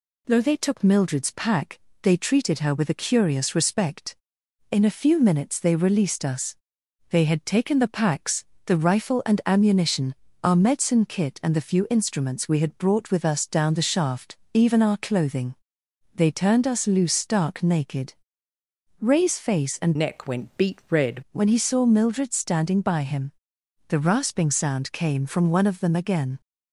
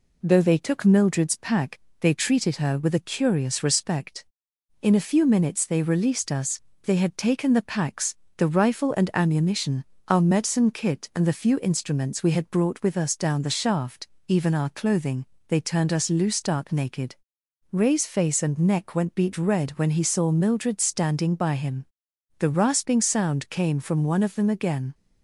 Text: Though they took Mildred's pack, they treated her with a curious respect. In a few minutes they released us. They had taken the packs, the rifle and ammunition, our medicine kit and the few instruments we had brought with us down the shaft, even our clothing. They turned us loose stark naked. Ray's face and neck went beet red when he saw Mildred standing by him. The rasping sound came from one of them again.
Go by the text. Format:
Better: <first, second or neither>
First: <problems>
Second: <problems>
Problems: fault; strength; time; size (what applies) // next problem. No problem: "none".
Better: second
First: changes voice from "neck" to "red"; from 19.9 to 21.2 s; 1.3 s long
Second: none